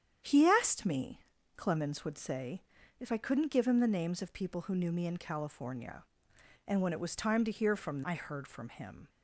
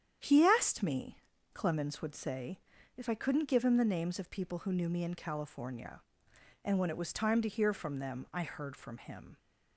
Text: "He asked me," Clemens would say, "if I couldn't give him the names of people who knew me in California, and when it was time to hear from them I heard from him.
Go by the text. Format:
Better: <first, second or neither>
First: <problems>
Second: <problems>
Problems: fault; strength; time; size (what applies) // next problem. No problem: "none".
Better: second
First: starts louder than the rest; strong; until 1.5 s; 9 dB // skips "them"; at 8.0 s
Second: starts louder than the rest; strong; until 1.6 s; 9 dB